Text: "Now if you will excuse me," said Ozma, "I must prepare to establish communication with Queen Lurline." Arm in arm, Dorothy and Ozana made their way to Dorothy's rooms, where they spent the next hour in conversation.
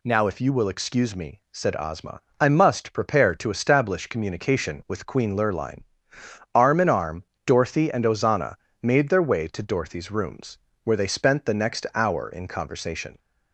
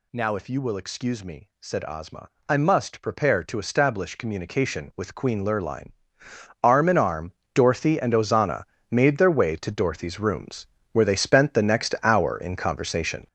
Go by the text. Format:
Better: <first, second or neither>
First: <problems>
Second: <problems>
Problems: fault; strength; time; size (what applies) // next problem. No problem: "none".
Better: first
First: pauses between "Ozana" and "made"; slight; at 8.5 s; 0.26 s long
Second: gets louder; strong; throughout; 8.5 dB // pauses between "Ozana" and "made"; slight; at 8.6 s; 0.26 s long